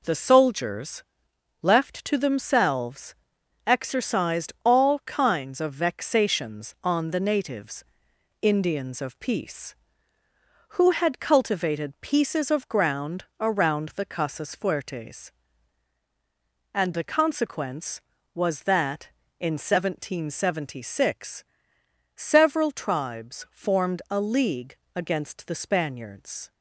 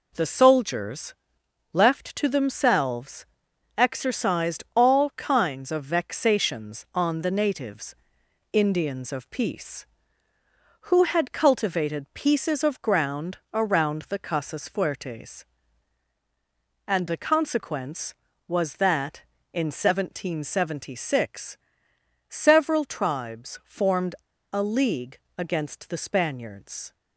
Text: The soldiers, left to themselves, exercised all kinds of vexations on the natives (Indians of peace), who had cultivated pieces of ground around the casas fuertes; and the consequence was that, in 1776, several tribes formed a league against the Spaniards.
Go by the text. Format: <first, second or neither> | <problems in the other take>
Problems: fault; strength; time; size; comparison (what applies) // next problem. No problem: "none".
first | pauses between "ground" and "around"; slight; at 13.3 s; 0.16 s long; slight in the first // pauses between "formed" and "a"; at 24.1 s; 0.37 s long // pauses between "league" and "against"; slight; at 25.1 s; 0.18 s long; slight in the first